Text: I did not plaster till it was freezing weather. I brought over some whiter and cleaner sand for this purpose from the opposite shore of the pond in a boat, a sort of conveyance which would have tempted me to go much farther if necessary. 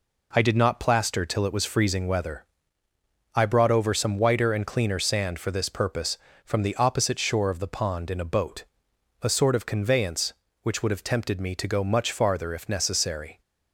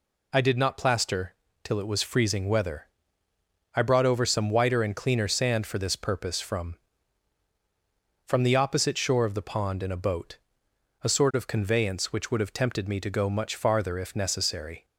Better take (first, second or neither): first